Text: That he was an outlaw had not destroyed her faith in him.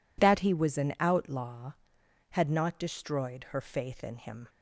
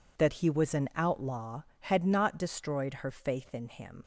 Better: first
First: none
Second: leaves "him" unfinished; at 4.0 s; 90 ms

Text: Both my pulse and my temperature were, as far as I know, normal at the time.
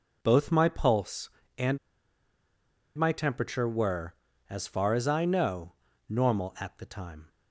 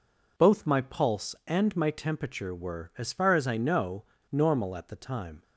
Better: second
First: pauses between "and" and "my"; at 1.7 s; 1.1 s long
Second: none

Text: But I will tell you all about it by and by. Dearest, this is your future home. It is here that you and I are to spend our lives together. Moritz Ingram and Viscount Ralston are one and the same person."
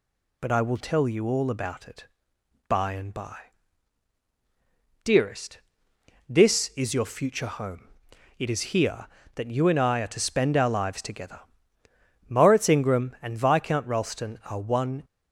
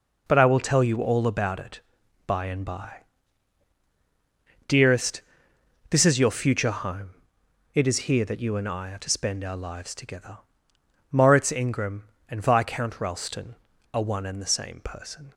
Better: second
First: stops before "and the same person"; at 15.0 s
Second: none

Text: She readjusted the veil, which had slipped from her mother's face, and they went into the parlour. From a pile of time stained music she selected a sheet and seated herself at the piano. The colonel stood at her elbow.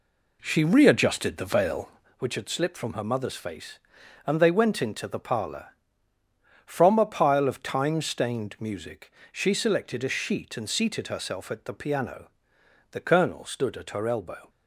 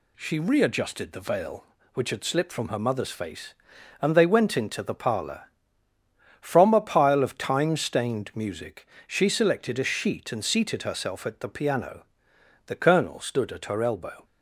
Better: second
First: starts louder than the rest; slight; until 2.2 s; 3 dB // pauses between "music" and "she"; slight; at 9.1 s; 0.20 s long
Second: pauses between "music" and "she"; slight; at 8.8 s; 0.20 s long

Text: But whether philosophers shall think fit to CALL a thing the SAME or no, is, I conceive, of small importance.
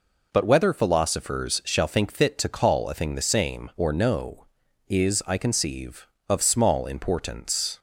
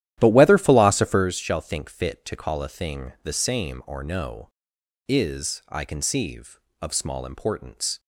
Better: first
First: none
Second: starts louder than the rest; strong; until 1.3 s; 12 dB

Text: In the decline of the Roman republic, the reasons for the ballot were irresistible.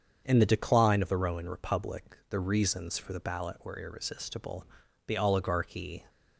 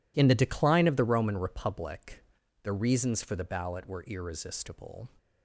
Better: second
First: starts louder than the rest; strong; until 1.2 s; 7 dB // goes on to say "The oligarchy"; noticeable; from 5.0 s on; 0.98 s long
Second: none

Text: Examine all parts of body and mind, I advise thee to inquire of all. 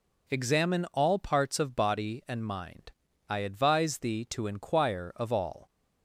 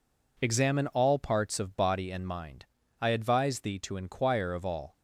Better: neither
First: none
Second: none

